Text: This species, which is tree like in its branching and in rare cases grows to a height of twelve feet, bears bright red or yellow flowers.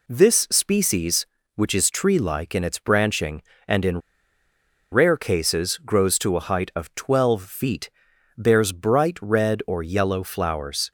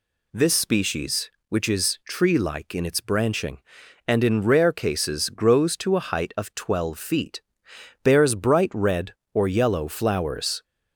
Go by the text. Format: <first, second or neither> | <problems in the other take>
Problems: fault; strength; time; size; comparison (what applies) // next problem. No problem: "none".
second | pauses between "in" and "rare"; noticeable; at 4.0 s; 0.92 s long